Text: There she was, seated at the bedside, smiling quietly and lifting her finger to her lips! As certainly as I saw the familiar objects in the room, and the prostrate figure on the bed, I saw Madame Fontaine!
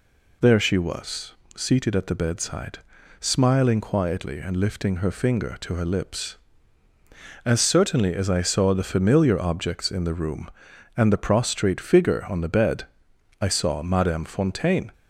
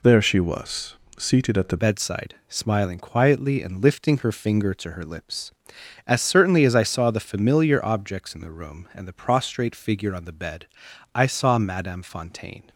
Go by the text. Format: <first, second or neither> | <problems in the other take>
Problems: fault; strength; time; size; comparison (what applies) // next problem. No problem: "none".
first | changes voice at "bedside"; from 1.7 s on; 10.9 s long